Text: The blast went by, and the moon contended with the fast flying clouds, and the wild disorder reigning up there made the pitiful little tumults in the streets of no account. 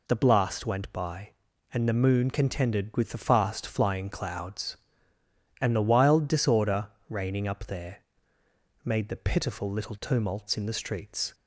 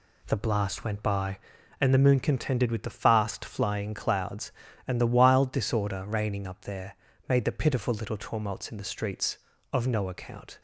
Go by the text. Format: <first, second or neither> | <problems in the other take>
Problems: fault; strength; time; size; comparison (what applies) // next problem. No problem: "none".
second | pauses between "disorder" and "reigning"; slight; at 6.8 s; 0.20 s long // pauses between "there" and "made"; noticeable; at 8.0 s; 0.82 s long; slight in the second // stops before "of no account"; at 11.3 s